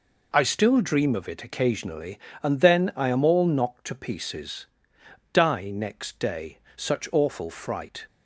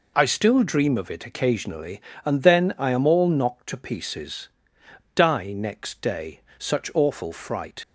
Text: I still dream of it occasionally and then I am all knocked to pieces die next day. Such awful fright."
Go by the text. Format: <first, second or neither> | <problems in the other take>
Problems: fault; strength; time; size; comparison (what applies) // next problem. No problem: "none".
first | pauses between "pieces" and "die"; noticeable; at 4.4 s; 0.68 s long; noticeable in the first // leaves "fright" unfinished; at 7.8 s; 40 ms